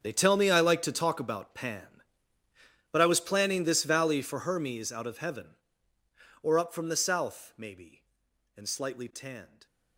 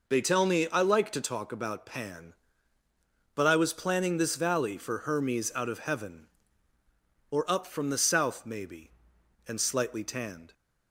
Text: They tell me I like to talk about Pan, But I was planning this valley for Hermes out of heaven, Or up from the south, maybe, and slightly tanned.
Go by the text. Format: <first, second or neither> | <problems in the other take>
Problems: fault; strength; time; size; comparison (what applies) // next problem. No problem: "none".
second | gets quieter; strong; throughout; 17 dB